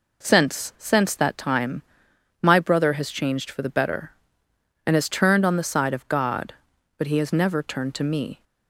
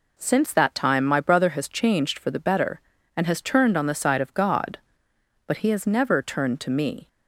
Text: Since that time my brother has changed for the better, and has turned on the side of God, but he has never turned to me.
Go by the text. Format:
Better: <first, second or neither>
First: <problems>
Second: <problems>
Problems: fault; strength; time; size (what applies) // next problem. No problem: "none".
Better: second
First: says "Since" twice; at 0.7 s // pauses between "time" and "my"; noticeable; at 1.8 s; 0.62 s long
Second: none